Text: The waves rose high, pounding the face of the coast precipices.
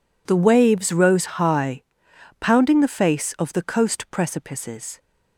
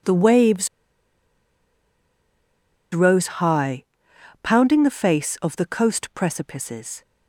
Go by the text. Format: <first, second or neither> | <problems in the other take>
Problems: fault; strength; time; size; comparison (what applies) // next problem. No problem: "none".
first | pauses between "waves" and "rose"; strong; at 0.6 s; 2.2 s long